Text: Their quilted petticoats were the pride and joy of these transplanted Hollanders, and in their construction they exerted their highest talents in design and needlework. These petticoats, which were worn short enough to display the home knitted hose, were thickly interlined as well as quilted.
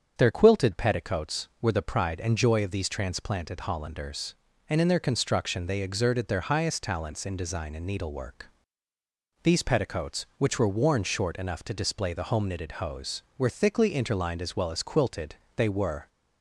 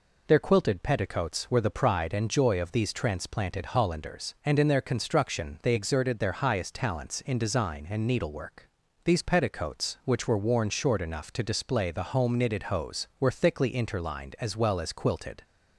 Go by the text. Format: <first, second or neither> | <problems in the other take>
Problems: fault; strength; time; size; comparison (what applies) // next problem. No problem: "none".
second | starts louder than the rest; strong; until 1.1 s; 7.5 dB // goes on to say "They were"; from 15.5 s on; 0.52 s long